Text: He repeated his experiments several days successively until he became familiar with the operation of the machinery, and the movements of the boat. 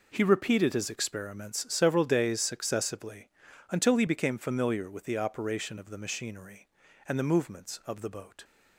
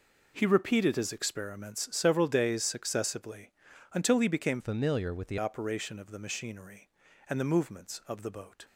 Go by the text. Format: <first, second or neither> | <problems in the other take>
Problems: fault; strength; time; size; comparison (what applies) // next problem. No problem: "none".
first | pauses between "successively" and "until"; at 3.5 s; 0.42 s long; also in the first // changes voice from "familiar" to "the"; from 4.5 to 5.3 s; 0.8 s long